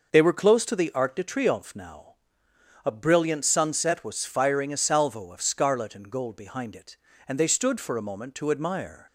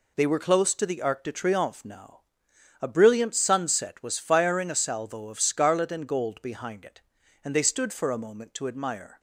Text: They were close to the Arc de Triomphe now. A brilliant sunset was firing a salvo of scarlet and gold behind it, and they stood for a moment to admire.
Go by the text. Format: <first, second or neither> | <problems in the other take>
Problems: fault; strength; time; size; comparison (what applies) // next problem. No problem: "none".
neither | none